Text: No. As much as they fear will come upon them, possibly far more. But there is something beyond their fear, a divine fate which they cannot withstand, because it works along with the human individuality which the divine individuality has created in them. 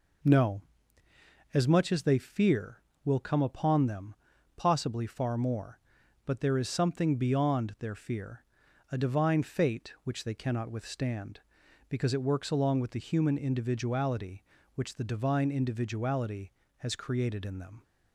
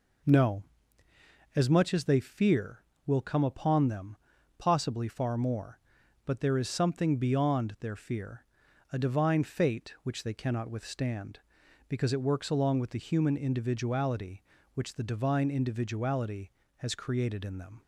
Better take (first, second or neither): neither